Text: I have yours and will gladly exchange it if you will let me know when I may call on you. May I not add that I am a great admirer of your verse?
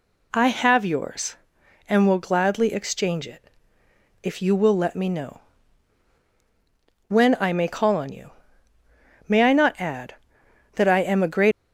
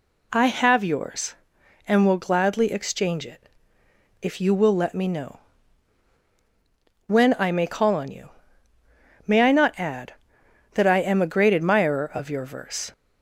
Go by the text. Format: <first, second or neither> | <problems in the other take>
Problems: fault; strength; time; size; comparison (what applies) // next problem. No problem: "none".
second | pauses between "it" and "if"; noticeable; at 3.5 s; 0.72 s long; noticeable in the second // pauses between "know" and "when"; strong; at 5.4 s; 1.6 s long; strong in the second // stops before "admirer of your verse"; at 11.5 s